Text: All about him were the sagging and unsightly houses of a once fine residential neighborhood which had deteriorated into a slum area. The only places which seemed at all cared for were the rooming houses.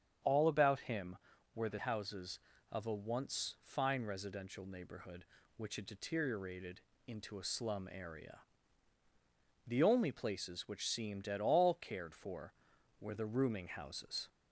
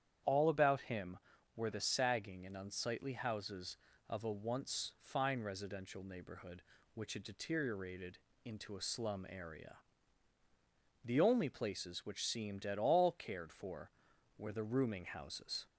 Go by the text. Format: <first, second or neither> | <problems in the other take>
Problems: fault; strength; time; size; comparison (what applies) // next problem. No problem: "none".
second | starts louder than the rest; strong; until 1.6 s; 8 dB; strong in the second // skips "sagging and unsightly"; at 1.7 s // pauses between "deteriorated" and "into"; slight; at 6.8 s; 0.26 s long; slight in the second